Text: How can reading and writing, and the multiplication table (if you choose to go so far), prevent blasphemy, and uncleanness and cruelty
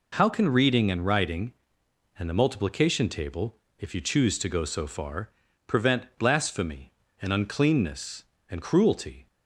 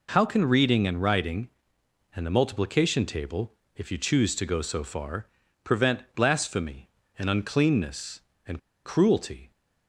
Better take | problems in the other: first | pauses between "prevent" and "blasphemy"; slight; at 5.9 s; 0.16 s long; slight in the first // pauses between "and" and "cruelty"; slight; at 8.5 s; 0.27 s long

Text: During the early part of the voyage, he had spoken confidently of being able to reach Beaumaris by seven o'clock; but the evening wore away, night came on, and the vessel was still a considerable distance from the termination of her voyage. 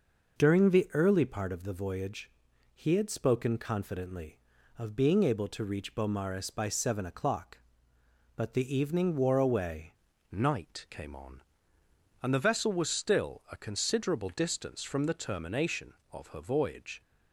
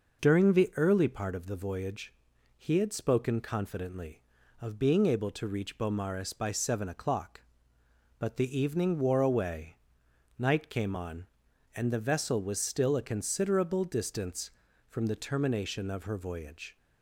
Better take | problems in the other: second | changes voice at "night"; from 10.3 s on; 6.7 s long

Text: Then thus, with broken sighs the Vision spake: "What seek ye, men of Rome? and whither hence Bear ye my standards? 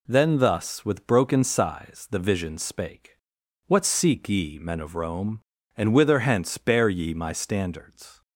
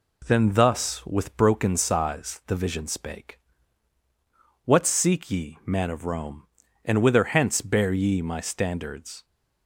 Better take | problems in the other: first | says "man" for "men"; at 5.6 s

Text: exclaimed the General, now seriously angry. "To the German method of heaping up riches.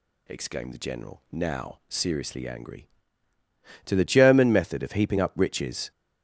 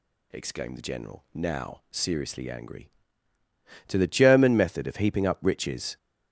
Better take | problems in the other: neither | none

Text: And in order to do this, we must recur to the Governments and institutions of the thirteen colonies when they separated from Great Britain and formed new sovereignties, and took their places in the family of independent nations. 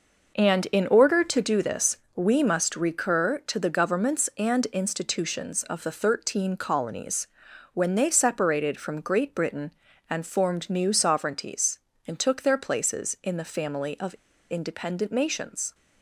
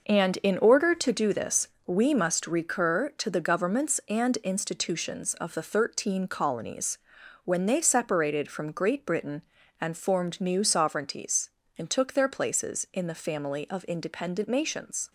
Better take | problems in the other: second | pauses between "colonies" and "when"; noticeable; at 7.2 s; 0.46 s long; noticeable in the second // pauses between "of" and "independent"; at 14.1 s; 0.36 s long

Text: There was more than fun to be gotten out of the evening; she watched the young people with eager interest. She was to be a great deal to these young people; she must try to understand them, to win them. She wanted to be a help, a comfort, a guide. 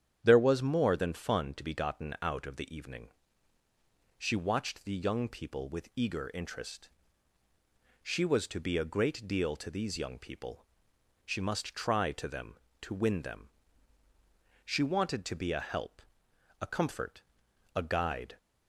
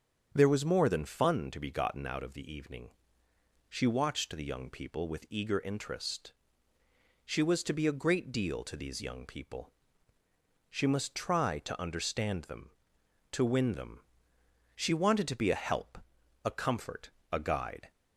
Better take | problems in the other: second | starts louder than the rest; strong; until 1.2 s; 9 dB; strong in the second // skips "understand"; at 12.2 s

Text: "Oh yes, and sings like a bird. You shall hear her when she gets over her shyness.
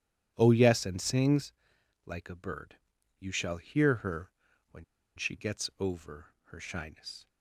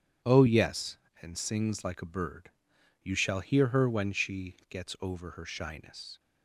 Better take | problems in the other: second | starts louder than the rest; strong; until 1.3 s; 10.5 dB // pauses between "sings" and "like"; noticeable; at 1.5 s; 0.54 s long // pauses between "her" and "when"; at 4.3 s; 0.40 s long // pauses between "when" and "she"; slight; at 4.8 s; 0.32 s long

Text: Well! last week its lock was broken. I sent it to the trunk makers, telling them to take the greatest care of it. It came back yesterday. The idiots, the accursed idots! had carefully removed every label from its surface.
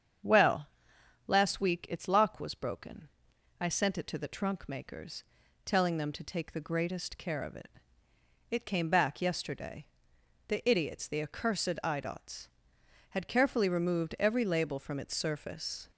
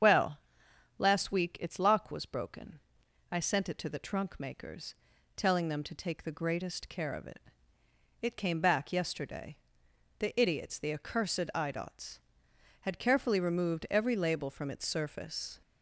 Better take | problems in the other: first | loses the start of "Well"; at 0.0 s; 80 ms // starts louder than the rest; strong; until 1.6 s; 8 dB; strong in the first

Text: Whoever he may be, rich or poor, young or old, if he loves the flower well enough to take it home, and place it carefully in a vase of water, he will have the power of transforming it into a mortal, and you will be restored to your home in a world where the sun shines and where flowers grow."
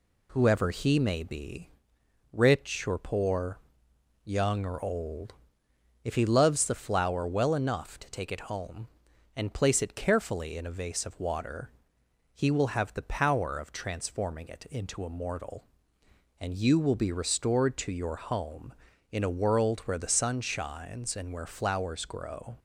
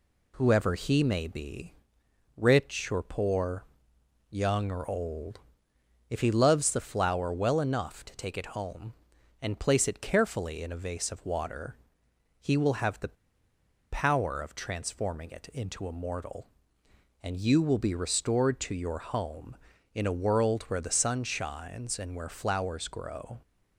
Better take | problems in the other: first | pauses between "the" and "power"; noticeable; at 13.1 s; 0.77 s long

